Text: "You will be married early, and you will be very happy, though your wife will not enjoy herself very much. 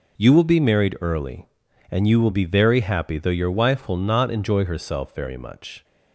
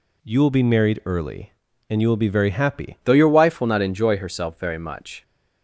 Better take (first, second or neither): first